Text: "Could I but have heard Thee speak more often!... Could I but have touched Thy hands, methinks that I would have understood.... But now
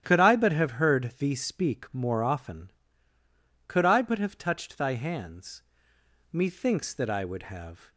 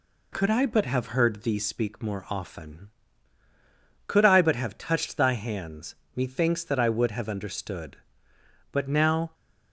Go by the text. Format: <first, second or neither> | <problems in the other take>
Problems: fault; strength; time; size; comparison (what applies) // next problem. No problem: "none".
second | starts louder than the rest; strong; until 1.0 s; 11 dB // stops before "understood But now"; at 7.9 s